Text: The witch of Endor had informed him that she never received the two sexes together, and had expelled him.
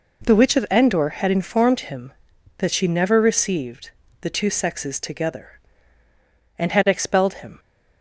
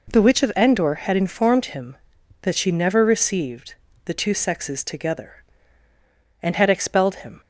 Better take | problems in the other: neither | pauses between "received" and "the"; slight; the same in both

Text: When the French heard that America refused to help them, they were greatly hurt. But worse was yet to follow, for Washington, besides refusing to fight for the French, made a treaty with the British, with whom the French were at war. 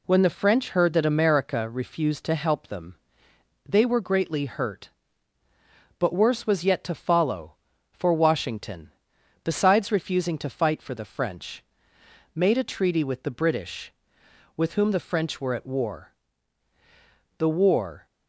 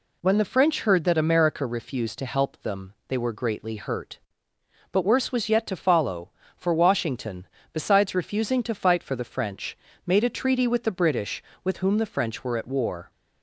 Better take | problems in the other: second | goes on to say "The War"; noticeable; from 17.3 s on; 0.66 s long

